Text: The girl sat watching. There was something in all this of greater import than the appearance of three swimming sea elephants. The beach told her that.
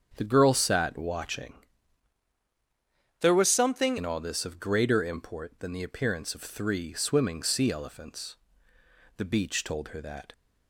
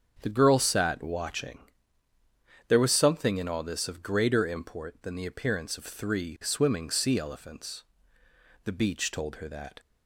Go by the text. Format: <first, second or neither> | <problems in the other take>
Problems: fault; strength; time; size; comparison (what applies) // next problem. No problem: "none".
second | starts louder than the rest; strong; until 1.1 s; 7.5 dB; strong in the second // changes voice from "There" to "something"; from 3.2 to 3.9 s; 0.7 s long